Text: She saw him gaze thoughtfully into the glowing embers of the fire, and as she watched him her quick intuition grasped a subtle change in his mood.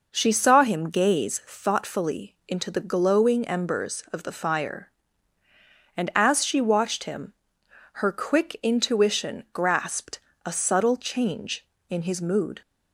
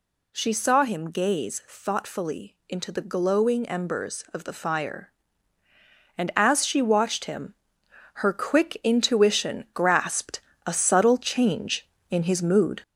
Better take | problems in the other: first | gets louder; noticeable; throughout; 4 dB // pauses between "him" and "her"; noticeable; at 7.5 s; 0.60 s long; noticeable in the first // pauses between "grasped" and "a"; slight; at 10.4 s; 0.26 s long; slight in the first

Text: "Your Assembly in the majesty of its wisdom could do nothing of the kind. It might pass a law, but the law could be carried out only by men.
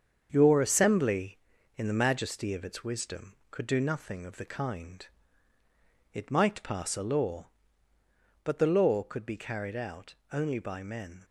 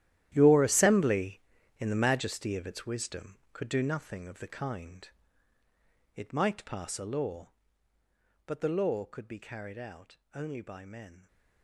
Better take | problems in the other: first | gets quieter; strong; throughout; 14.5 dB // starts louder than the rest; strong; until 1.3 s; 12.5 dB; strong in the first // pauses between "out" and "only"; slight; at 10.1 s; 0.16 s long; slight in the first

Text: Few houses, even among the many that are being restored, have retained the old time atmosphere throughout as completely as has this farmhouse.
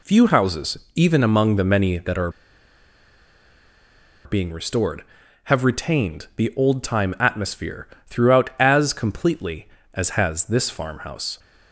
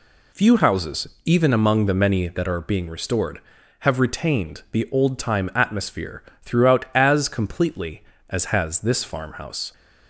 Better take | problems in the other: second | pauses between "are" and "being"; strong; at 2.2 s; 1.9 s long // pauses between "atmosphere" and "throughout"; slight; at 7.8 s; 0.18 s long; slight in the second

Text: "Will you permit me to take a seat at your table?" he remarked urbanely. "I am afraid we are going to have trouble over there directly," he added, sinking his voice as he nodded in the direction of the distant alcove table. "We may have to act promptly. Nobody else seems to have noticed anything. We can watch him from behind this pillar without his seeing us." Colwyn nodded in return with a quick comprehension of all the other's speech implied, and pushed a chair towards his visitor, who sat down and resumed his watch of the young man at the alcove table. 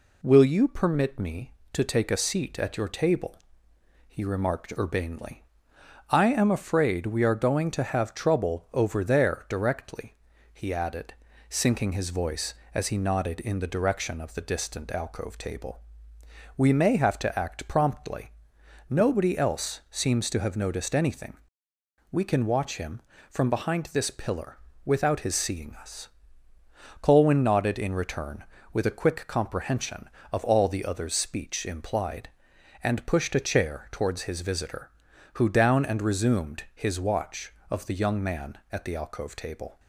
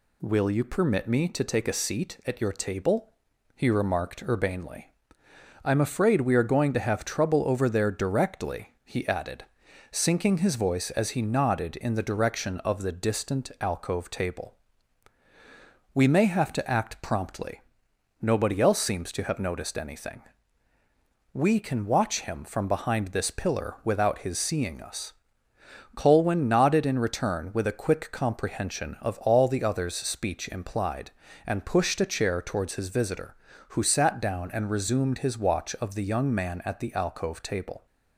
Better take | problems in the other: second | pauses between "pillar" and "without"; slight; at 24.5 s; 0.26 s long // skips "sat"; at 35.4 s

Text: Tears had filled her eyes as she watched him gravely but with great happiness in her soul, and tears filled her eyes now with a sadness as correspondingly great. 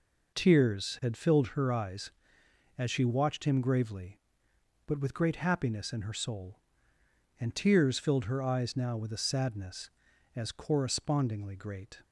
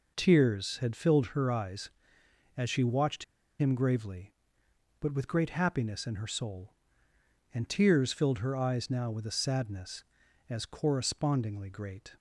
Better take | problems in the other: first | pauses between "watched" and "him"; slight; at 3.2 s; 0.35 s long

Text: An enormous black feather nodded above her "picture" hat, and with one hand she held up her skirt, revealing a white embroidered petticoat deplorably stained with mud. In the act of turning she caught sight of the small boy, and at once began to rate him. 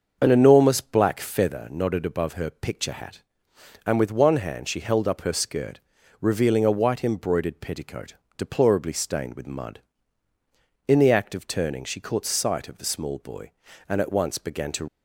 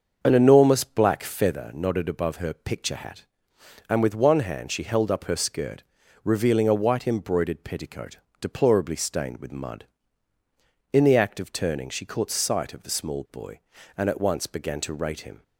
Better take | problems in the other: second | starts louder than the rest; until 1.2 s; 6.5 dB; also in the second // pauses between "petticoat" and "deplorably"; slight; at 8.1 s; 0.22 s long; slight in the second // stops before "rate him"; at 14.8 s

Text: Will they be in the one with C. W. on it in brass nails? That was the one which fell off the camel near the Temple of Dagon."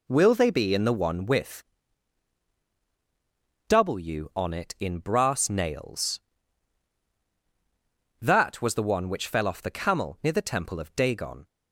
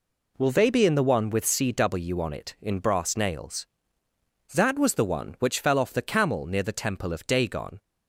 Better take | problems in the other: second | skips "C"; at 2.6 s

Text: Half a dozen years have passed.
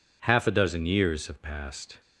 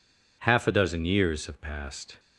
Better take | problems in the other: neither | none

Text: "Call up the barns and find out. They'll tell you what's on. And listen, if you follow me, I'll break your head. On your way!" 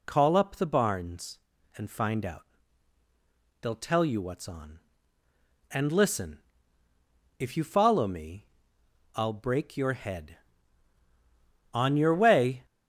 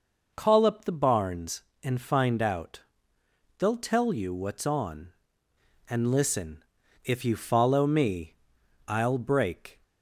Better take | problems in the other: first | stops before "your head On your way"; at 9.8 s

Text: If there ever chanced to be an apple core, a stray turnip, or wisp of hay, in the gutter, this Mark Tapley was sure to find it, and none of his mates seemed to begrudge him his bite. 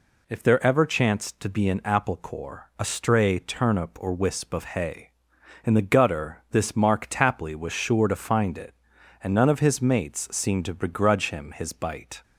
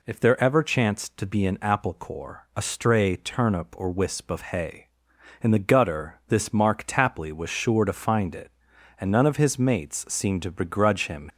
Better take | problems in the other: first | stops before "his bite"; at 11.2 s

